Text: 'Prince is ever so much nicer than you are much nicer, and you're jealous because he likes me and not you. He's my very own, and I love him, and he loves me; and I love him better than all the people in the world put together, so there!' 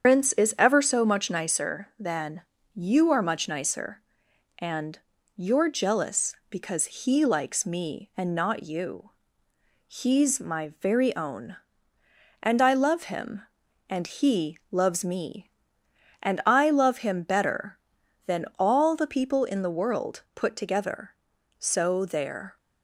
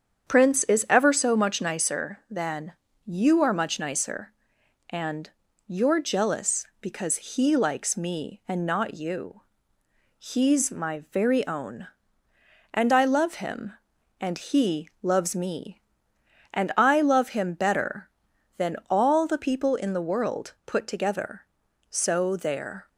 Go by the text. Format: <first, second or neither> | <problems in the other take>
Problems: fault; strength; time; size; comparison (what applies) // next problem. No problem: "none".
second | loses the start of "Prince"; at 0.0 s; 85 ms // starts louder than the rest; strong; until 1.0 s; 7.5 dB; strong in the second // pauses between "than" and "you"; slight; at 2.4 s; 0.32 s long; slight in the second // pauses between "and" and "you're"; at 4.9 s; 0.38 s long; also in the second